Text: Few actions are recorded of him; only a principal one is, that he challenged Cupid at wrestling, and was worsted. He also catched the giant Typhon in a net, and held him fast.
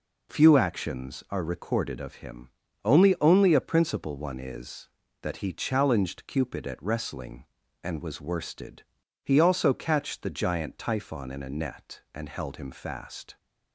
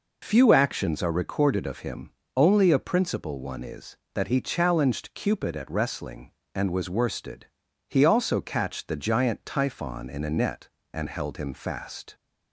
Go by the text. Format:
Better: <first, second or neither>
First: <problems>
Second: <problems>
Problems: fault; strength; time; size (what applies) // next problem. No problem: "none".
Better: second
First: says "only" twice; at 3.1 s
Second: none